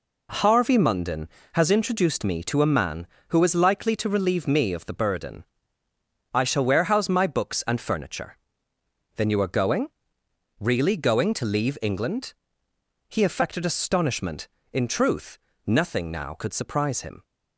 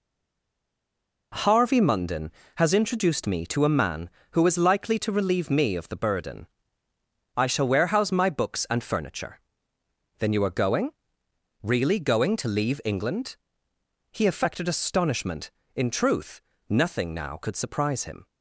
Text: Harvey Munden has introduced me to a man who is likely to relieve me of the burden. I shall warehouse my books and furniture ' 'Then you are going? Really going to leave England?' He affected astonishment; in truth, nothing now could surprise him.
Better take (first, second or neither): first